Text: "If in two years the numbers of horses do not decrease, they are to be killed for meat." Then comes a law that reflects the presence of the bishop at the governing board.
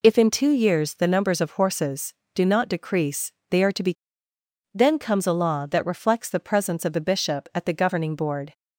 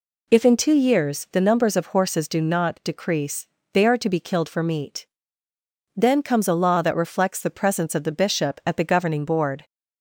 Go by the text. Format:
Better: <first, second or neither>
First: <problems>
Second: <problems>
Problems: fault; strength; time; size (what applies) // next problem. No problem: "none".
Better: second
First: skips "killed for meat"; at 4.3 s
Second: none